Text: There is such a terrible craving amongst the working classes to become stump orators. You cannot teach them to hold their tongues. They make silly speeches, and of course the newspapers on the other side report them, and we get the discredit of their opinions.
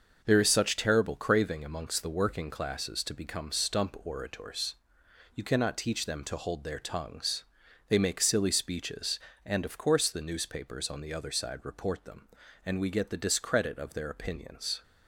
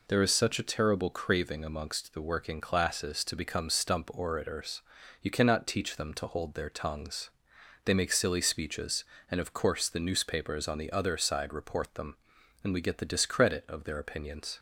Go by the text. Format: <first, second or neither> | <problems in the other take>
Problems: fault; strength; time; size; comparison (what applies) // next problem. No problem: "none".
second | skips "a"; at 0.7 s